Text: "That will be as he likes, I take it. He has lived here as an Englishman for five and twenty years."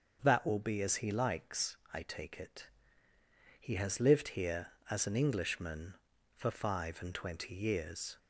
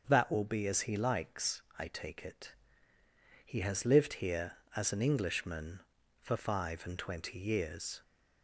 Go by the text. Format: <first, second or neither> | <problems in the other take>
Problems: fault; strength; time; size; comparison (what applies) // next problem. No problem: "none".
neither | starts louder than the rest; the same in both